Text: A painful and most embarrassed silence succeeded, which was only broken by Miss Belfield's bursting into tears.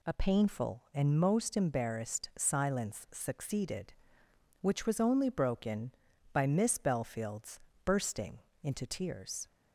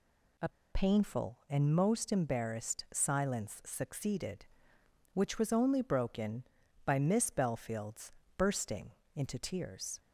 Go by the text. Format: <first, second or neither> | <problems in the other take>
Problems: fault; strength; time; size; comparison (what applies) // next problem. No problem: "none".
first | pauses between "A" and "painful"; slight; at 0.4 s; 0.23 s long // pauses between "Belfield's" and "bursting"; slight; at 8.1 s; 0.28 s long; slight in the first // pauses between "bursting" and "into"; slight; at 8.8 s; 0.26 s long; slight in the first